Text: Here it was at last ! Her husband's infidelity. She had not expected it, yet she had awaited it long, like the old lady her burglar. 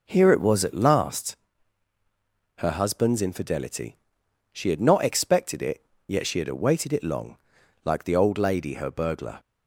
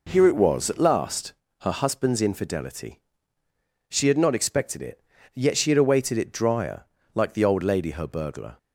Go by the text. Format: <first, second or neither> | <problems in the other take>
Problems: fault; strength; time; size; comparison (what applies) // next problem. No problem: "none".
first | says "drier" for "long"; at 6.3 s